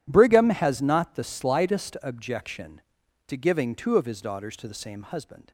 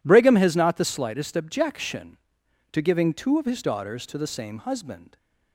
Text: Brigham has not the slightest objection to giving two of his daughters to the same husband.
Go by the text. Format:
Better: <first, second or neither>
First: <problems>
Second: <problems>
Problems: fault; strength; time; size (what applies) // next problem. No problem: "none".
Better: neither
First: none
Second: none